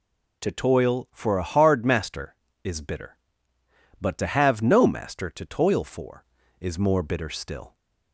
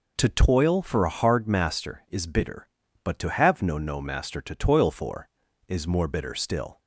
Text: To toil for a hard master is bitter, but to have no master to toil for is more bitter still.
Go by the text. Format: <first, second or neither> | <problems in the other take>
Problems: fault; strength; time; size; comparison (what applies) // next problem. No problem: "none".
first | says "no" twice; at 3.7 s